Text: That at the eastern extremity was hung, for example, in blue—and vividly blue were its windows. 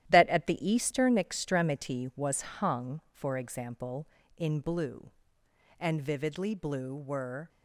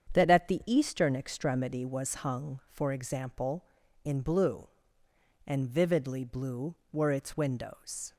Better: second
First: starts louder than the rest; strong; until 1.0 s; 12 dB // stops before "its windows"; at 7.4 s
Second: starts louder than the rest; strong; until 1.1 s; 8 dB

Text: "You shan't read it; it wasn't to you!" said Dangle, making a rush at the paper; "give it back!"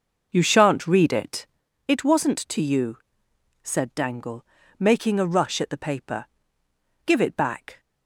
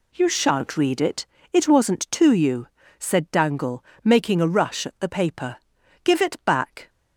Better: second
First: starts louder than the rest; noticeable; until 1.6 s; 5.5 dB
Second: none

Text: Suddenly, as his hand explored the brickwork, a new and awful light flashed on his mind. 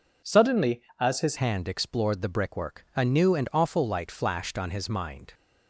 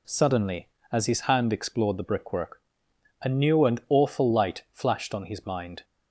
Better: second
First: changes voice at "hand"; from 1.3 s on; 4.0 s long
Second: none

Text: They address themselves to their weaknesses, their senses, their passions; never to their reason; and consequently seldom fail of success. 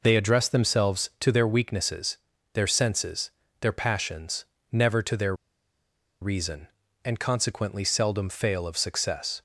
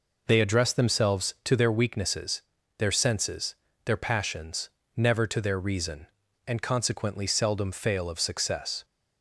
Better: second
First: pauses between "their" and "reason"; noticeable; at 5.3 s; 0.86 s long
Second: none

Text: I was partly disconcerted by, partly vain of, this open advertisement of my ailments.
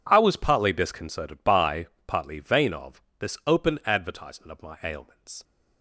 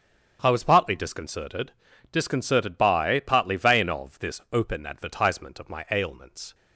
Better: first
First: none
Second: starts louder than the rest; strong; until 1.4 s; 8 dB // says "disconcerted" twice; at 2.1 s

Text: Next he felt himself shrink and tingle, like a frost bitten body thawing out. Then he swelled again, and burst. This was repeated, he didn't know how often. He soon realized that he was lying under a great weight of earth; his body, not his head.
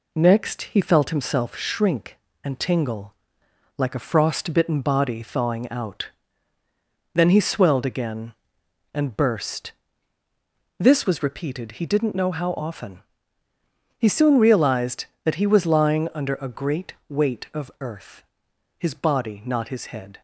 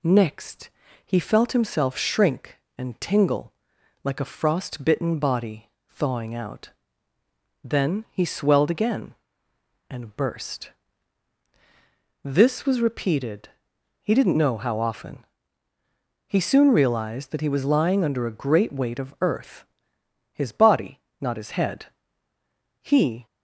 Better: first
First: none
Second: pauses between "Next" and "he"; slight; at 0.6 s; 0.36 s long // pauses between "body" and "thawing"; slight; at 5.6 s; 0.20 s long // goes on to say "He"; slight; from 22.8 s on; 0.44 s long

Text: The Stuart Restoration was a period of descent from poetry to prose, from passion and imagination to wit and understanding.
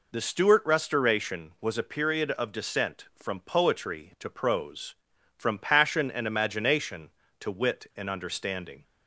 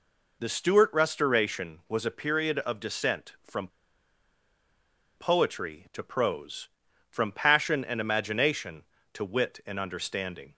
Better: first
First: none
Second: pauses between "from" and "poetry"; strong; at 3.6 s; 1.4 s long

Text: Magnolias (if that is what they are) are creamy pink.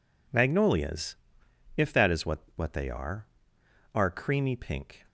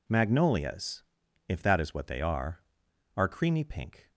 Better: second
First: says "what" twice; at 2.5 s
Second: none

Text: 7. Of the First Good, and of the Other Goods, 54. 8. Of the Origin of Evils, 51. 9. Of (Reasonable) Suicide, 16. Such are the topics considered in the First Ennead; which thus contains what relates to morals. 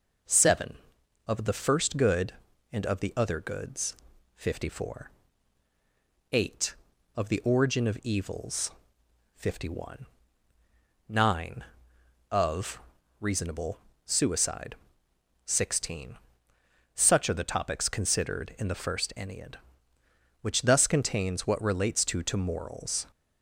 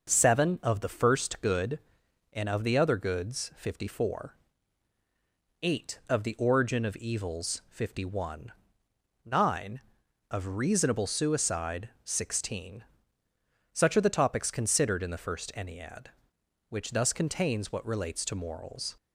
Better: second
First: says "to" twice; at 22.2 s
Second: none

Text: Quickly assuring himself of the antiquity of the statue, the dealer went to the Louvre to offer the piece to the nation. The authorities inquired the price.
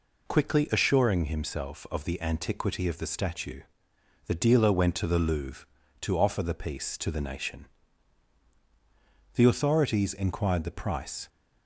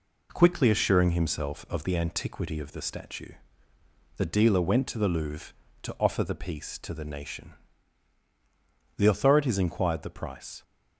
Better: neither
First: none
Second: none

